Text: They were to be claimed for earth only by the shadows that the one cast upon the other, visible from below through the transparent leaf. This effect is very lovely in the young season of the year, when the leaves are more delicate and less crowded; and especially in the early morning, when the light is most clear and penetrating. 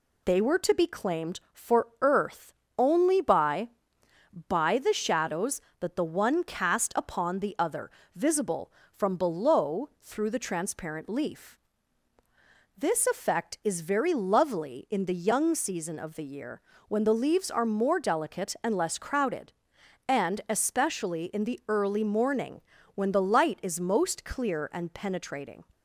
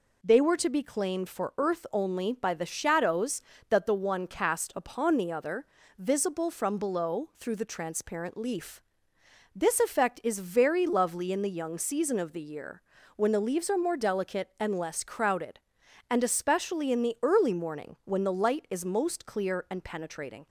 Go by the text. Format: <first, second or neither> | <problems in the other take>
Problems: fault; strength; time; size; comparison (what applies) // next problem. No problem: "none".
second | pauses between "earth" and "only"; slight; at 2.5 s; 0.24 s long // says "by" twice; at 4.4 s